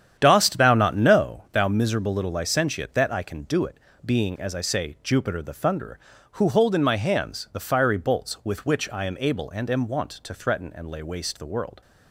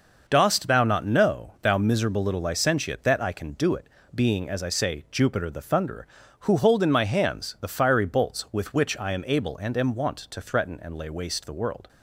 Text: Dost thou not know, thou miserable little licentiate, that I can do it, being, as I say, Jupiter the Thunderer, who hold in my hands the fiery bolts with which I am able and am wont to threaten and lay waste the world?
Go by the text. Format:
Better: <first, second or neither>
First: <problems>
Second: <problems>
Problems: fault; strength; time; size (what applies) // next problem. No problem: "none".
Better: second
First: starts louder than the rest; strong; until 1.6 s; 9 dB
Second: none